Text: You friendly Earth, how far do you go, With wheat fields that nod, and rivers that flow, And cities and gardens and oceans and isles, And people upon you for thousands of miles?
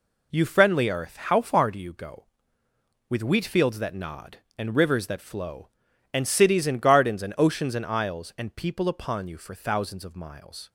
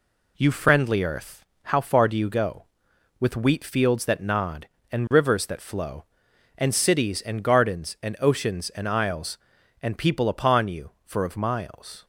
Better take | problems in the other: first | skips "thousands"; at 11.2 s

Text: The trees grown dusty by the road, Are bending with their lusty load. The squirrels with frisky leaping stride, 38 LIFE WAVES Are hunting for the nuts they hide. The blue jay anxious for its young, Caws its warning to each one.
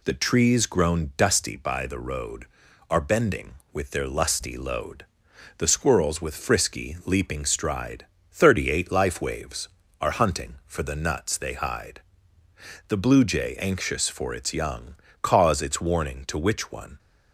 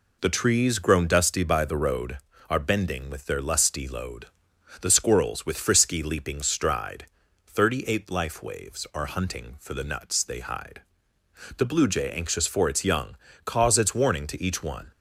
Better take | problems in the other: second | says "which" for "each"; at 16.3 s

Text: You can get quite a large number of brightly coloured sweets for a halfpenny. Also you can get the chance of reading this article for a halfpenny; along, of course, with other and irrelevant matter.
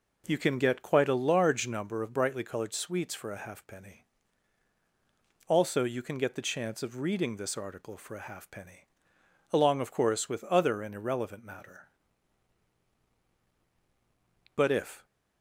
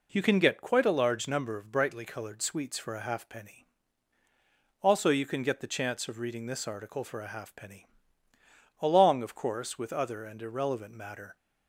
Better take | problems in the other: second | goes on to say "But if"; from 14.5 s on; 0.50 s long

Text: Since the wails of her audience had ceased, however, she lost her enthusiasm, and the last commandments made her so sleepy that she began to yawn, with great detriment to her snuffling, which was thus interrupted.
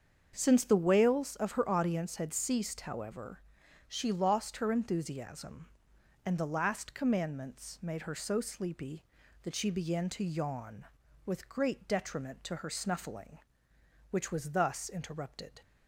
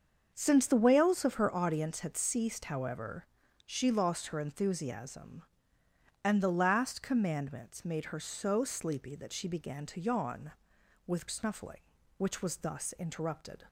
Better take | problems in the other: first | starts louder than the rest; until 1.3 s; 6.5 dB; also in the first // skips "great detriment to her"; at 11.2 s

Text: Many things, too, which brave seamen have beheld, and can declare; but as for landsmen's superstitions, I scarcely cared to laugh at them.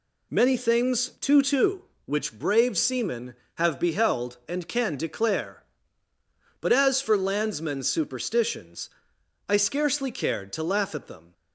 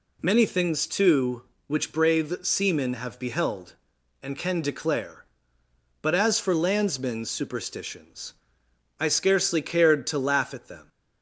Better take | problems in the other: second | says "too" twice; at 1.4 s

